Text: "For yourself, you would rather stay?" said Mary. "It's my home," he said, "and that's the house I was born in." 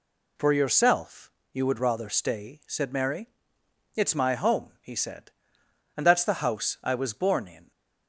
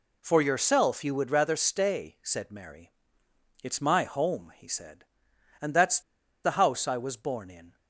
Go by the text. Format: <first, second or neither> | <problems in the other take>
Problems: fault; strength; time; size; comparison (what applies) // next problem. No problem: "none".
first | pauses between "that's" and "the"; at 6.0 s; 0.43 s long